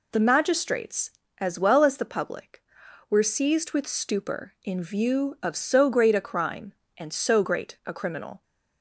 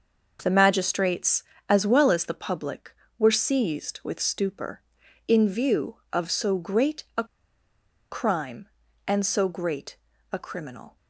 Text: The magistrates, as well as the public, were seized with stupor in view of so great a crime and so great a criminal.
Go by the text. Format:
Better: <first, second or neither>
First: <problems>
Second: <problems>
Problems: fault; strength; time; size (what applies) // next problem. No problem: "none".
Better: first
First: none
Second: pauses between "a" and "crime"; noticeable; at 7.2 s; 0.86 s long // pauses between "great" and "a"; slight; at 9.9 s; 0.36 s long